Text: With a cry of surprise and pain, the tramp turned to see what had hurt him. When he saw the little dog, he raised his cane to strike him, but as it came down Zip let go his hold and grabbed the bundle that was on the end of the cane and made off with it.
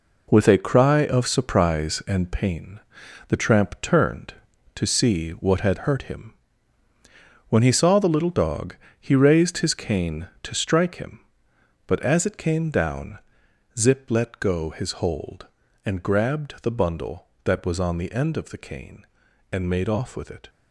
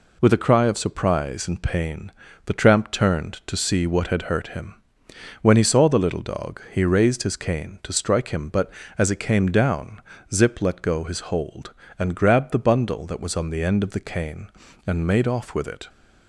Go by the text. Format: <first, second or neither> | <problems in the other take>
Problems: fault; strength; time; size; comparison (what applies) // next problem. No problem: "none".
second | gets quieter; strong; throughout; 8.5 dB // pauses between "down" and "Zip"; noticeable; at 13.1 s; 0.58 s long; slight in the second